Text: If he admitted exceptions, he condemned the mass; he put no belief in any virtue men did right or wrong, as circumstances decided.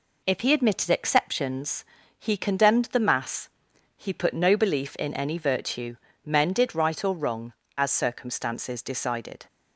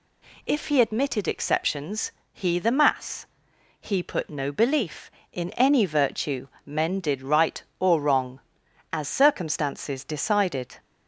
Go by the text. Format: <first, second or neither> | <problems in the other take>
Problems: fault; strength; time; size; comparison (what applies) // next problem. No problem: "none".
first | skips "condemned"; at 2.5 s // pauses between "virtue" and "men"; slight; at 6.4 s; 0.18 s long; slight in the first